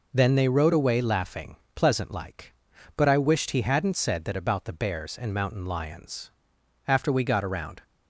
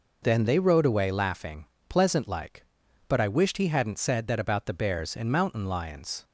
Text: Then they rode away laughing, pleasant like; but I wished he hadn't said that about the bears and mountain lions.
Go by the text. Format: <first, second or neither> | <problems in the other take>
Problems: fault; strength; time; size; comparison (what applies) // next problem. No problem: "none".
second | goes on to say "After we got around"; noticeable; from 6.8 s on; 0.98 s long